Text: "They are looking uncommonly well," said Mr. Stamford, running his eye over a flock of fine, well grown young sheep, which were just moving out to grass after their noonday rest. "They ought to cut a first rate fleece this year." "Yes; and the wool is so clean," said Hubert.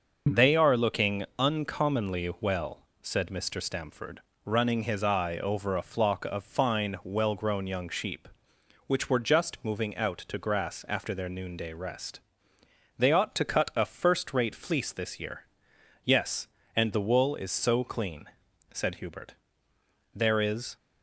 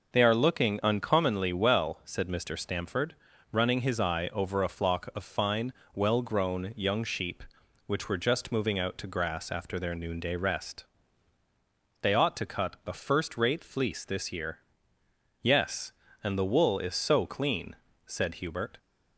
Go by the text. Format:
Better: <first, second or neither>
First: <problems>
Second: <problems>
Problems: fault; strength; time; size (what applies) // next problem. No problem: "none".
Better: second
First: starts louder than the rest; noticeable; until 1.5 s; 6 dB // pauses between "looking" and "uncommonly"; slight; at 1.2 s; 0.16 s long // goes on to say "There is"; noticeable; from 20.1 s on; 0.62 s long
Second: none